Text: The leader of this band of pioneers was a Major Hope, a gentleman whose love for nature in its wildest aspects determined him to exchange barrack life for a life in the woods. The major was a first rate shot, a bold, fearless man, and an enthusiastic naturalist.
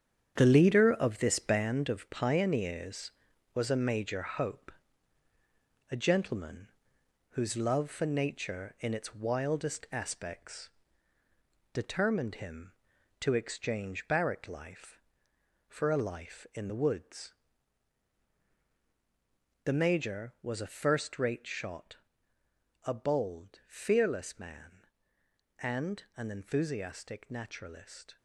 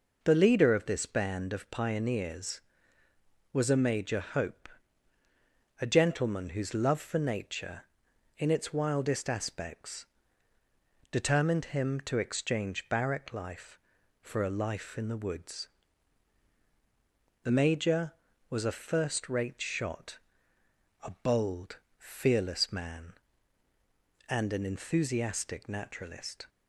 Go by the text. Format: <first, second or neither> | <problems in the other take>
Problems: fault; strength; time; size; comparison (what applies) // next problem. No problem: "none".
second | gets quieter; strong; throughout; 9.5 dB // pauses between "gentleman" and "whose"; noticeable; at 6.6 s; 0.62 s long // pauses between "aspects" and "determined"; at 10.6 s; 1.0 s long; also in the second